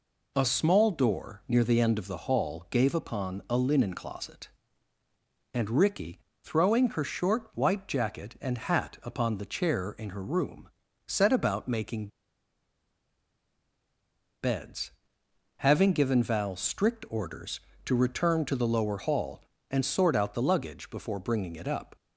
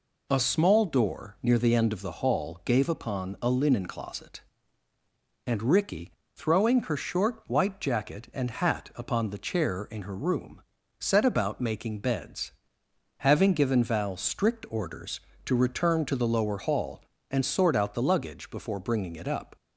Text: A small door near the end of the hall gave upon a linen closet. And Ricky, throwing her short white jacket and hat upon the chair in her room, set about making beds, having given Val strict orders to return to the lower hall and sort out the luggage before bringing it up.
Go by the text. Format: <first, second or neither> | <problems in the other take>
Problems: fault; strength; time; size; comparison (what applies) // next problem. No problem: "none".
second | pauses between "making" and "beds"; strong; at 12.0 s; 2.3 s long